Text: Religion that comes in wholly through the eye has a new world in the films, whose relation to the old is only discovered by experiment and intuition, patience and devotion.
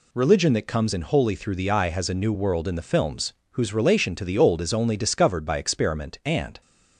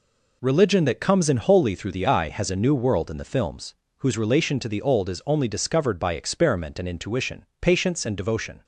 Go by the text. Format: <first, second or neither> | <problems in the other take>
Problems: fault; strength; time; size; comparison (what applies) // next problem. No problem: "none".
second | stops before "intuition patience and devotion"; at 6.6 s